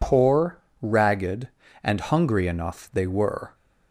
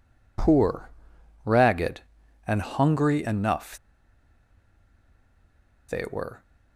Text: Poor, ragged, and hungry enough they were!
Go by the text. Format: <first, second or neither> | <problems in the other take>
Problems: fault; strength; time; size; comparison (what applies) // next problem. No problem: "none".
first | pauses between "enough" and "they"; strong; at 3.7 s; 2.1 s long